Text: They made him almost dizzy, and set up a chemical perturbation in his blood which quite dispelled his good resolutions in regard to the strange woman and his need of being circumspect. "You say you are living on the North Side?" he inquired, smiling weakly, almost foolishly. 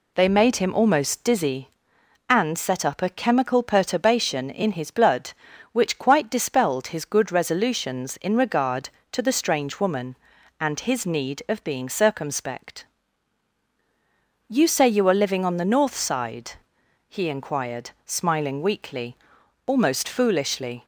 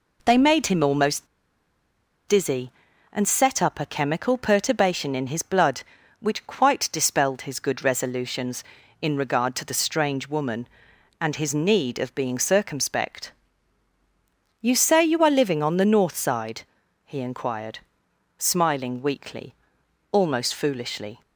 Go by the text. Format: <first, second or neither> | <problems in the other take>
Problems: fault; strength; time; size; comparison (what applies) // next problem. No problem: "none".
first | pauses between "almost" and "dizzy"; at 1.2 s; 1.0 s long